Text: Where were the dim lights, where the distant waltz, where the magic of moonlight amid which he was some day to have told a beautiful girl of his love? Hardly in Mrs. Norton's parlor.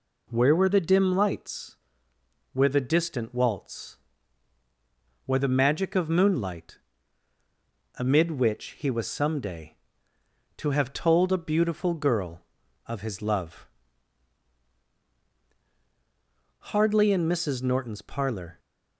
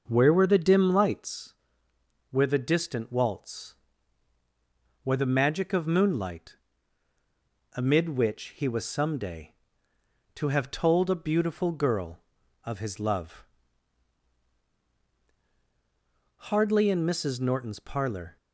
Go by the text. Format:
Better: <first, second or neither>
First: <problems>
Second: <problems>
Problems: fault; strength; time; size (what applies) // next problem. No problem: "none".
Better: first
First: pauses between "moonlight" and "amid"; at 6.7 s; 1.2 s long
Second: starts louder than the rest; noticeable; until 1.4 s; 6 dB // pauses between "moonlight" and "amid"; at 6.5 s; 1.2 s long